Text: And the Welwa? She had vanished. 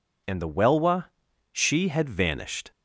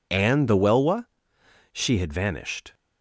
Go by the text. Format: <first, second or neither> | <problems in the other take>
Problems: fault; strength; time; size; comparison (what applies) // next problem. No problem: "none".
neither | none